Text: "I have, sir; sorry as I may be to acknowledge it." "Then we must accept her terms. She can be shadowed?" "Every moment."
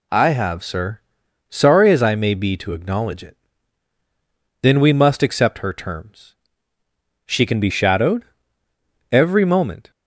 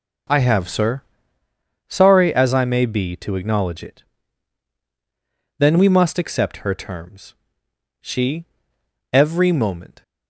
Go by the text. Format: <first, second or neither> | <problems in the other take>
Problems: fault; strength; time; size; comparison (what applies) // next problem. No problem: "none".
first | skips "can be shadowed"; at 8.7 s